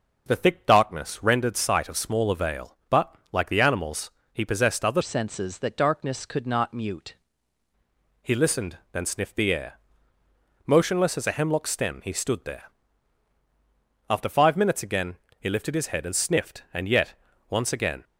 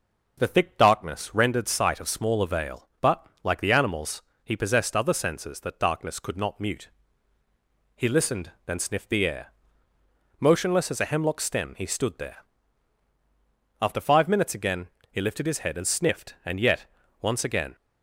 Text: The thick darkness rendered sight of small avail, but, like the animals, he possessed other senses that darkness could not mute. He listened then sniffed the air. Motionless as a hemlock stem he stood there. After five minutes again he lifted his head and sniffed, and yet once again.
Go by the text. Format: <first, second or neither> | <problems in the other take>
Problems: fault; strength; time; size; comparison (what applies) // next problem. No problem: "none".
second | changes voice from "senses" to "mute"; from 5.0 to 7.1 s; 2.1 s long // pauses between "listened" and "then"; slight; at 8.7 s; 0.16 s long; slight in the second // pauses between "again" and "he"; slight; at 15.1 s; 0.22 s long; slight in the second // pauses between "yet" and "once"; slight; at 17.1 s; 0.36 s long; slight in the second